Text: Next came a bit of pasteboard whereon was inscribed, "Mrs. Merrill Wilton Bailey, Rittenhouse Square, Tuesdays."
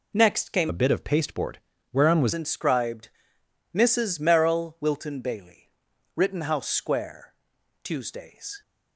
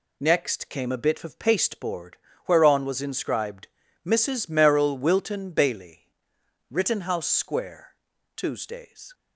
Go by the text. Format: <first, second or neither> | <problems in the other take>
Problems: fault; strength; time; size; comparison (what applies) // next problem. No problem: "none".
second | changes voice from "a" to "was"; from 0.6 to 2.3 s; 1.7 s long // pauses between "pasteboard" and "whereon"; slight; at 1.5 s; 0.32 s long; slight in the second